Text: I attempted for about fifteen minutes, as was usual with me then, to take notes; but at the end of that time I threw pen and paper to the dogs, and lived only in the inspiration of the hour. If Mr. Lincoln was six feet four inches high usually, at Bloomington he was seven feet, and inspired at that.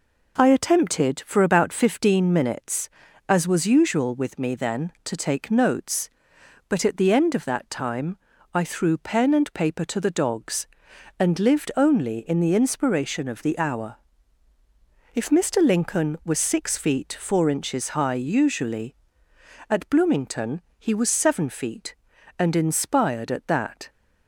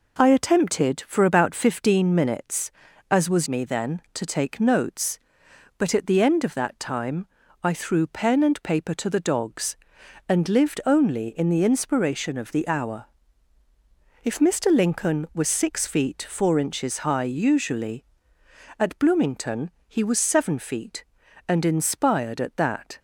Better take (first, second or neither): first